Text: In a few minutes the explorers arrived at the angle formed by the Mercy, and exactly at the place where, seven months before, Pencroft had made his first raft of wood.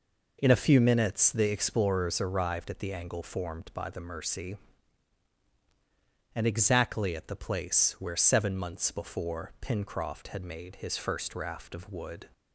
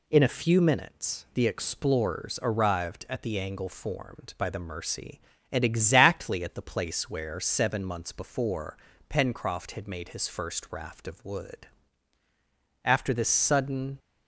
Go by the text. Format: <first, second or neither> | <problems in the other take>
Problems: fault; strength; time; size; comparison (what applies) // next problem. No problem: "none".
first | goes on to say "After this sudden"; noticeable; from 12.8 s on; 1.1 s long